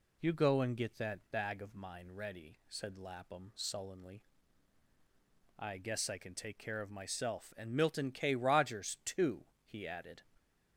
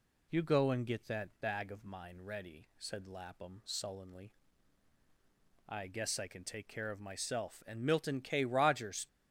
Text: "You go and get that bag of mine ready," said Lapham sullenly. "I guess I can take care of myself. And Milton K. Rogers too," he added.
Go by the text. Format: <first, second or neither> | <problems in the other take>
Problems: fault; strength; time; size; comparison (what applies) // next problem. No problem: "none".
first | stops before "too he added"; at 9.0 s